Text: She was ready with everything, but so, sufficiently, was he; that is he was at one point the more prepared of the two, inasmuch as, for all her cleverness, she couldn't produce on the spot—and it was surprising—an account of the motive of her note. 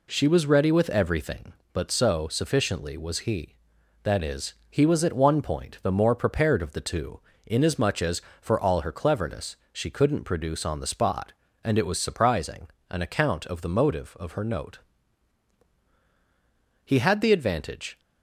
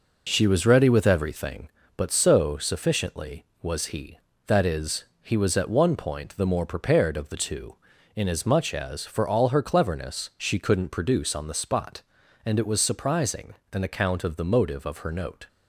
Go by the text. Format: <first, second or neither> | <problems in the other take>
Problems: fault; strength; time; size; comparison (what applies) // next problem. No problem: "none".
second | pauses between "is" and "he"; slight; at 4.5 s; 0.16 s long; slight in the second // goes on to say "He had the advantage"; noticeable; from 16.8 s on; 1.1 s long